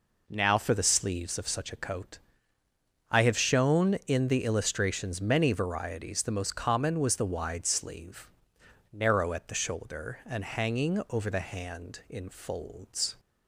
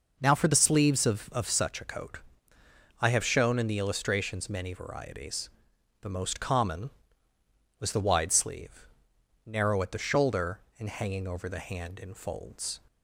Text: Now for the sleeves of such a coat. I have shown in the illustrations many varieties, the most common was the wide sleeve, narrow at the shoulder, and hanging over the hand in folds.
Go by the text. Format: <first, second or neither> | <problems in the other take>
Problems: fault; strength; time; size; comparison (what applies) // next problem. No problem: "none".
first | says "of" twice; at 1.3 s